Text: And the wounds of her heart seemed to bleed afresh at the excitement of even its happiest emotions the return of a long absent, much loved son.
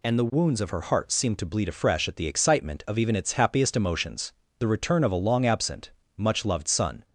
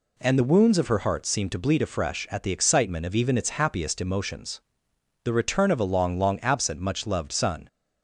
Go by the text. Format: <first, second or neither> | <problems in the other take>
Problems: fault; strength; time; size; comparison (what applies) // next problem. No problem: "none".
first | pauses between "emotions" and "the"; noticeable; at 4.5 s; 0.65 s long; slight in the first // says "long" twice; at 6.1 s